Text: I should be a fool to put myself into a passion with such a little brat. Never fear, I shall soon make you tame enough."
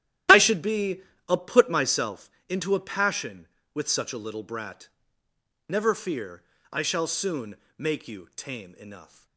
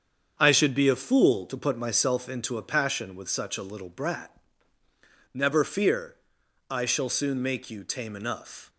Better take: second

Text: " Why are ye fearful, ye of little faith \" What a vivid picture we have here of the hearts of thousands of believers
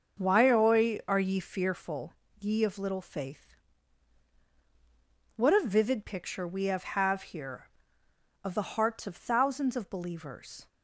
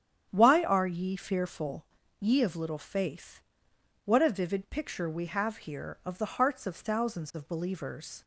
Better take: second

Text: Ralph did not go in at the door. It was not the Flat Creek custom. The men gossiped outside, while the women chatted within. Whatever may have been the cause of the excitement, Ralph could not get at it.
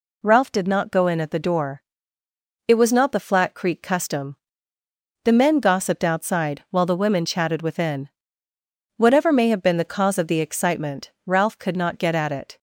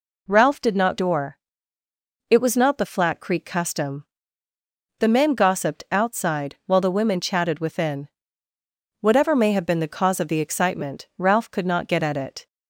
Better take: first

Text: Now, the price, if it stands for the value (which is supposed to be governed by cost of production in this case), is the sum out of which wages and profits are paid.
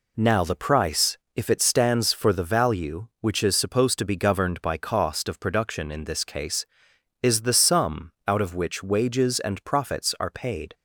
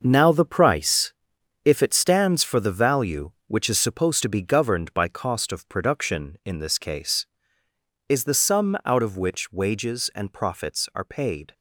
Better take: first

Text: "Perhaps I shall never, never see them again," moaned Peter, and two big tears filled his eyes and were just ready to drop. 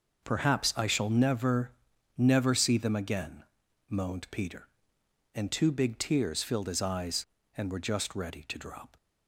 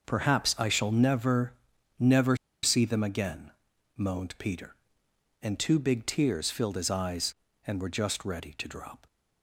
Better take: first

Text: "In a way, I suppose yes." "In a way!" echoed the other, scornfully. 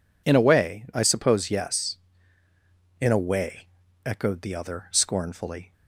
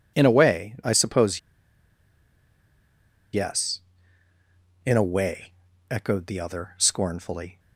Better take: first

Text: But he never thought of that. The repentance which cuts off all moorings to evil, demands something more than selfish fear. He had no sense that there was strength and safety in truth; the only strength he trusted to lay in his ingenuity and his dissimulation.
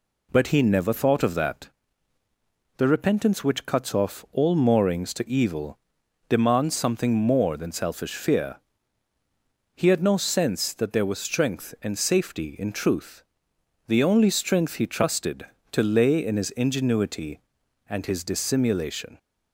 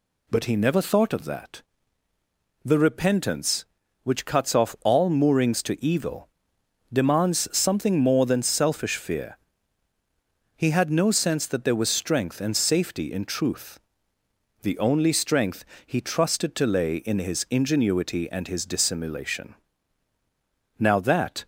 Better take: first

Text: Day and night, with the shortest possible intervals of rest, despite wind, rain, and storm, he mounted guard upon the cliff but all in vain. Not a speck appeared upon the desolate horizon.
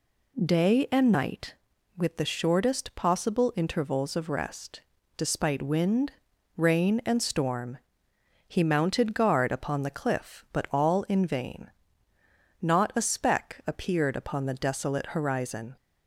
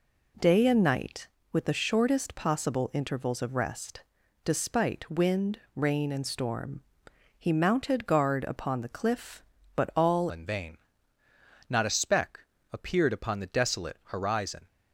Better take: first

